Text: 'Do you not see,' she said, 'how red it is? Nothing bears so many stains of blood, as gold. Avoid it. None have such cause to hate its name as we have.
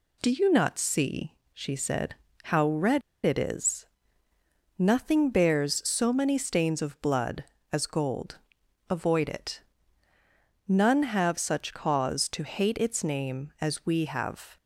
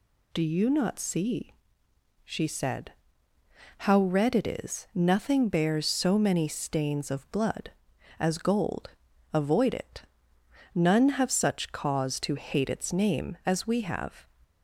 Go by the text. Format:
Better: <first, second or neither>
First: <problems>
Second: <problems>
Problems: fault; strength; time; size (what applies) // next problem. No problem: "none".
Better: second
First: pauses between "red" and "it"; slight; at 3.0 s; 0.25 s long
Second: none